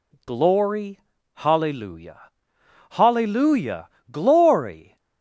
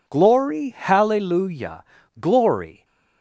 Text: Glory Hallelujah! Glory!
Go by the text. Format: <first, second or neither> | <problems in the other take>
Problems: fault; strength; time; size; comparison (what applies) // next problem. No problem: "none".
second | pauses between "Glory" and "Hallelujah"; slight; at 0.9 s; 0.34 s long // says "Hallelujah" twice; at 2.9 s